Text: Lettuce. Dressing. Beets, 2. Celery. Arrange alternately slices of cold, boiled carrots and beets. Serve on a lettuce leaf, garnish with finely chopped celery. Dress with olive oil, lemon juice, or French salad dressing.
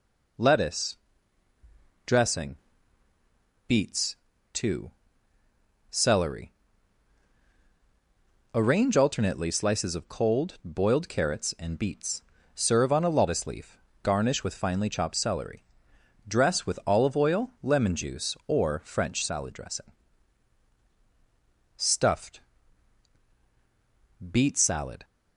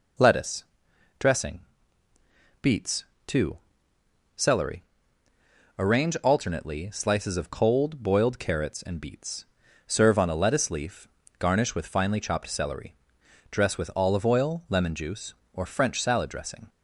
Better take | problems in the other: second | goes on to say "STUFFED BEET SALAD"; strong; from 21.7 s on; 3.2 s long

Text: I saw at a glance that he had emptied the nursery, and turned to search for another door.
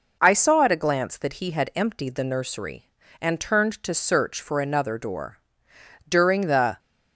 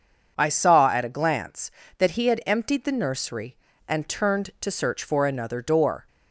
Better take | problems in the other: second | goes on to say "During the"; noticeable; from 6.0 s on; 0.70 s long

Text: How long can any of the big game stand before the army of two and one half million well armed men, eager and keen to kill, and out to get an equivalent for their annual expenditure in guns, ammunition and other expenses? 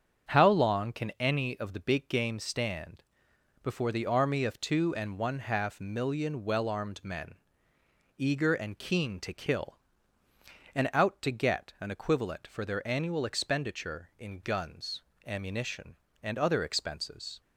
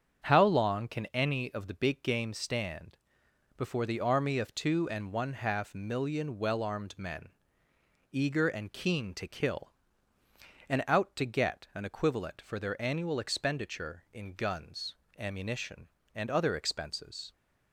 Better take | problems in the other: neither | starts louder than the rest; strong; the same in both // pauses between "stand" and "before"; noticeable; the same in both

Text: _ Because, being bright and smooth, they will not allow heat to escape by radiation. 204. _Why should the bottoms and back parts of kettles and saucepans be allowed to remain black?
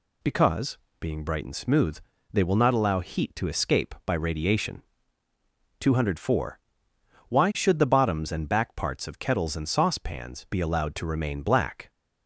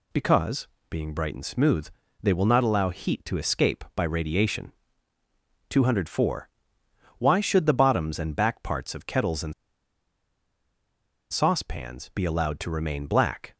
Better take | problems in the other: first | pauses between "and" and "saucepans"; strong; at 9.5 s; 1.7 s long

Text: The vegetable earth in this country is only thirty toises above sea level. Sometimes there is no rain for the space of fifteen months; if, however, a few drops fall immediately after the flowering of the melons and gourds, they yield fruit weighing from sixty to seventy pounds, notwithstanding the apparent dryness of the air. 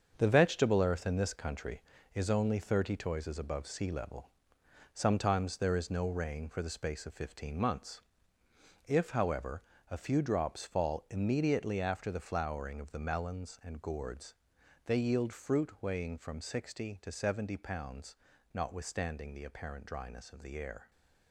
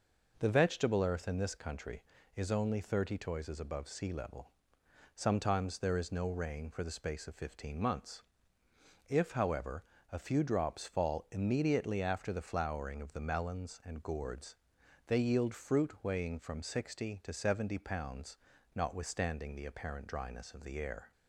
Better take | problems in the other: second | gets quieter; strong; throughout; 8.5 dB

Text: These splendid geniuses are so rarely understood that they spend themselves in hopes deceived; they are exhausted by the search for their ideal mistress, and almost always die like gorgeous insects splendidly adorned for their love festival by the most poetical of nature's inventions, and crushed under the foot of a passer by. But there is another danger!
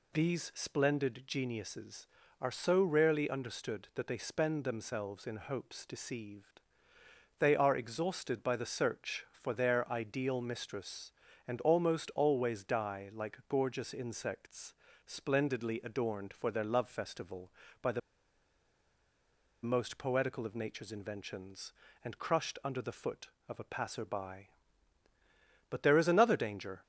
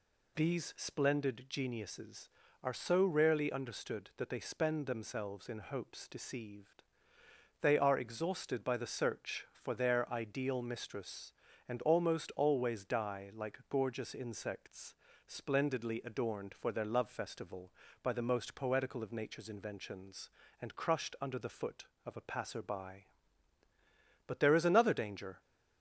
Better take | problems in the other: second | pauses between "insects" and "splendidly"; slight; at 14.7 s; 0.32 s long; slight in the second // pauses between "the" and "most"; strong; at 18.0 s; 1.6 s long

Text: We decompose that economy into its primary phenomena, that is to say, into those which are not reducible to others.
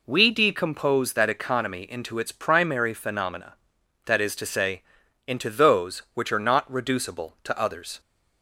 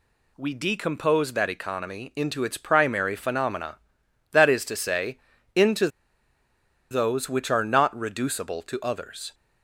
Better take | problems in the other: first | pauses between "into" and "those"; at 5.8 s; 1.0 s long

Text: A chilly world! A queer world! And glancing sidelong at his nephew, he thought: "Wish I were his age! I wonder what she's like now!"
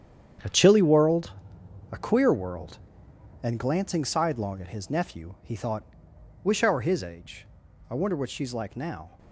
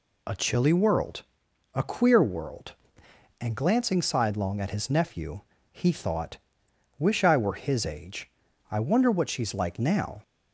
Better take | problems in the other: second | gets quieter; strong; throughout; 11 dB

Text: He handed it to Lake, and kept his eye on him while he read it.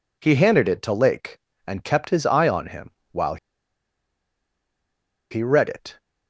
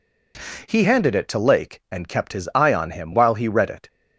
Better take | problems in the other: second | pauses between "him" and "while"; slight; at 2.8 s; 0.22 s long // pauses between "while" and "he"; strong; at 3.3 s; 1.9 s long

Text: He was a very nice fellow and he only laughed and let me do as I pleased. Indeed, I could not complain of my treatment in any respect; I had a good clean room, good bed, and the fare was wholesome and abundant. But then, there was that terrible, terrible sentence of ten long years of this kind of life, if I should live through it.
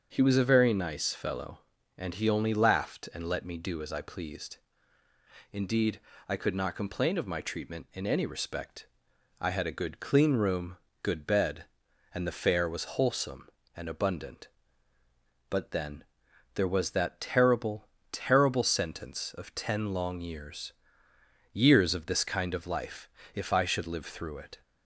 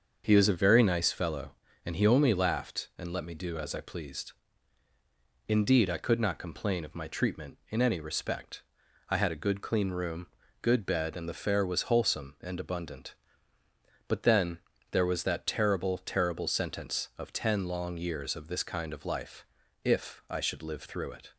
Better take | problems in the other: second | starts louder than the rest; until 1.1 s; 6.5 dB; also in the second // says "years" twice; at 21.5 s

